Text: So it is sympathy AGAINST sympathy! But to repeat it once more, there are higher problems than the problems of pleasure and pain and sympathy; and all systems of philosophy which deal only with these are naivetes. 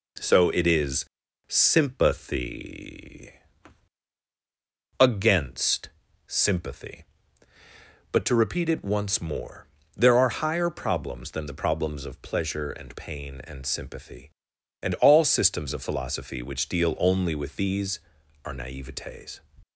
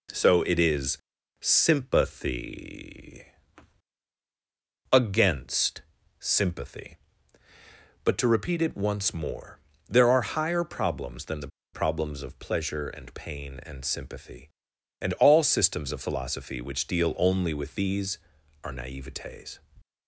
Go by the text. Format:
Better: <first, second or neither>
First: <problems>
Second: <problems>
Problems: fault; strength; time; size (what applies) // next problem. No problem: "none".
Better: first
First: pauses between "is" and "sympathy"; at 1.0 s; 0.42 s long // pauses between "sympathy" and "AGAINST"; strong; at 3.3 s; 1.6 s long // pauses between "AGAINST" and "sympathy"; slight; at 5.8 s; 0.36 s long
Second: pauses between "is" and "sympathy"; at 0.9 s; 0.42 s long // pauses between "sympathy" and "AGAINST"; strong; at 3.2 s; 1.6 s long // pauses between "AGAINST" and "sympathy"; slight; at 5.8 s; 0.36 s long // pauses between "the" and "problems"; slight; at 11.4 s; 0.25 s long